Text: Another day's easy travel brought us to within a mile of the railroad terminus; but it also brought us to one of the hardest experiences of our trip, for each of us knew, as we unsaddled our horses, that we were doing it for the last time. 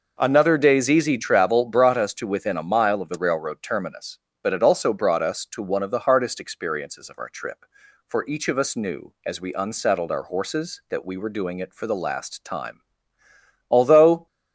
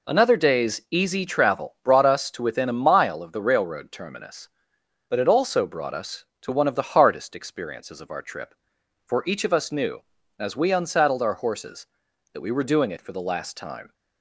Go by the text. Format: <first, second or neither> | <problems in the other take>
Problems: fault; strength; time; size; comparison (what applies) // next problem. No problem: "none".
second | goes on to say "Although"; from 13.7 s on; 0.56 s long